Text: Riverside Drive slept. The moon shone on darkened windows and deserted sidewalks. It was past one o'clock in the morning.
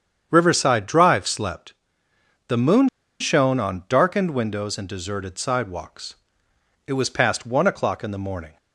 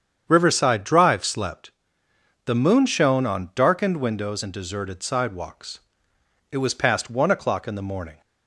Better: second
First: starts louder than the rest; strong; until 1.3 s; 8 dB // pauses between "moon" and "shone"; slight; at 2.8 s; 0.32 s long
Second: starts louder than the rest; strong; until 1.2 s; 8 dB

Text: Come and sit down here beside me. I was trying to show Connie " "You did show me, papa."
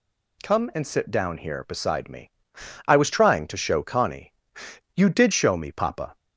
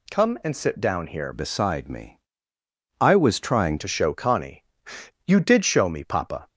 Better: first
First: none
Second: changes voice from "beside" to "trying"; from 1.3 to 3.7 s; 2.4 s long

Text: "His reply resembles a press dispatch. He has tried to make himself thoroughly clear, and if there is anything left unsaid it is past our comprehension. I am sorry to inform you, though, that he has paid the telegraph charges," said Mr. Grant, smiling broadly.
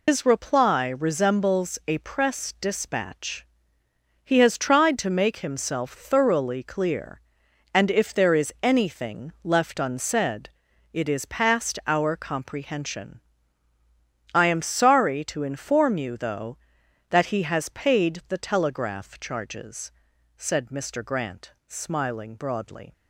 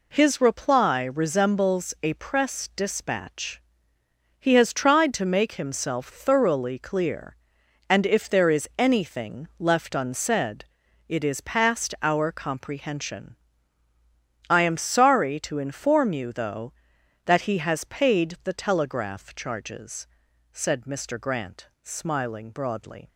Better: second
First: loses the start of "His"; at 0.0 s; 115 ms // pauses between "unsaid" and "it"; at 10.5 s; 0.42 s long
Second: pauses between "unsaid" and "it"; at 10.6 s; 0.42 s long

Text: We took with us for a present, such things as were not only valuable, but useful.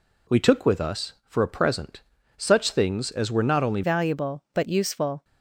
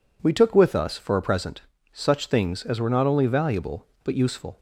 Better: second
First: changes voice at "valuable"; from 3.8 s on; 1.4 s long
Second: none

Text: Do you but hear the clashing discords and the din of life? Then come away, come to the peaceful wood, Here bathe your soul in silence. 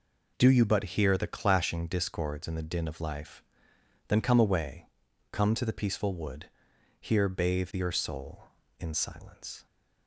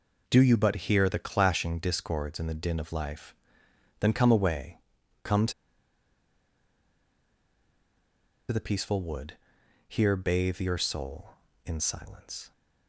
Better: first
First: none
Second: pauses between "to" and "the"; strong; at 5.5 s; 2.9 s long

